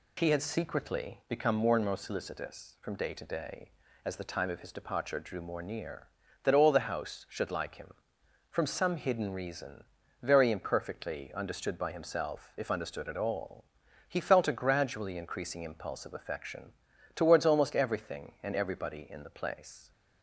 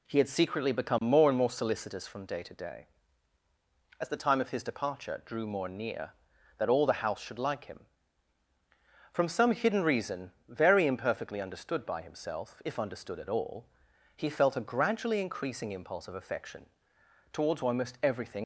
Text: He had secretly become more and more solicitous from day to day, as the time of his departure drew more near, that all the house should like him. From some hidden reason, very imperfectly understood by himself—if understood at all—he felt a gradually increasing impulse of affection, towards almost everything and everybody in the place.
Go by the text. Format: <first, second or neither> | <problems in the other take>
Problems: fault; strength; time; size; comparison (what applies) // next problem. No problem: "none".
first | stops before "and everybody in the place"; at 18.4 s